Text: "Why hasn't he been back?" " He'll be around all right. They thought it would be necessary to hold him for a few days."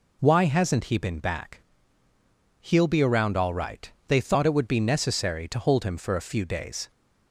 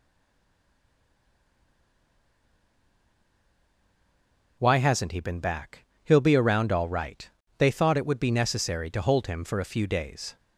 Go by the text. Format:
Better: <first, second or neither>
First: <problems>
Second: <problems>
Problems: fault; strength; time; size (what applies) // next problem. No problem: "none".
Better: first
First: none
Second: stays silent before the first word; strong; until 4.5 s; 4.5 s long